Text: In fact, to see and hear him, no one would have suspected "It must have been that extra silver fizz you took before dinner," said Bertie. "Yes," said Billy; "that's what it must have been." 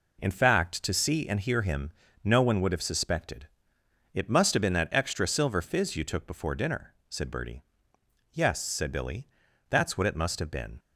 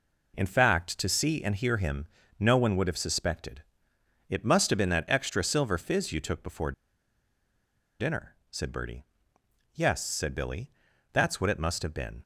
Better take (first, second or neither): first